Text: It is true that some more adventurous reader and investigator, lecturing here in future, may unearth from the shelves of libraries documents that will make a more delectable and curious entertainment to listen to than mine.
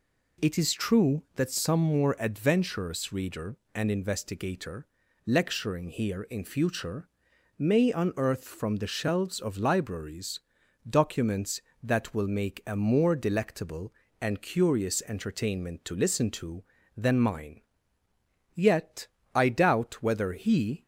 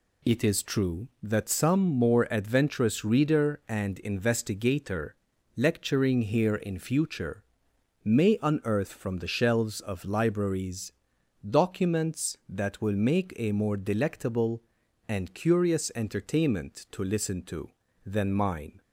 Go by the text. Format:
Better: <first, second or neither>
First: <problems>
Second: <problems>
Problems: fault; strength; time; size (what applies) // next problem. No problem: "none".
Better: second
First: pauses between "libraries" and "documents"; noticeable; at 10.3 s; 0.50 s long // goes on to say "Yet I doubt whether he"; strong; from 18.5 s on; 2.3 s long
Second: pauses between "libraries" and "documents"; noticeable; at 10.9 s; 0.56 s long